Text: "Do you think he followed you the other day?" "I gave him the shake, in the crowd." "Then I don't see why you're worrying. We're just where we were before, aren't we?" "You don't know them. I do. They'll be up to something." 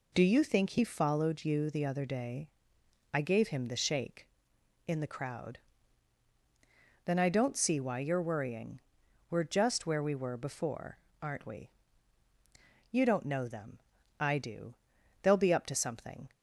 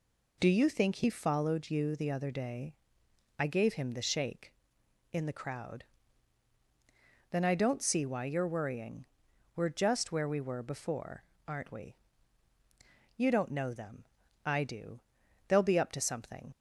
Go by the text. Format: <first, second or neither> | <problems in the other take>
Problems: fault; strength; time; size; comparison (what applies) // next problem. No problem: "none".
first | leaves "something" unfinished; at 16.5 s; 45 ms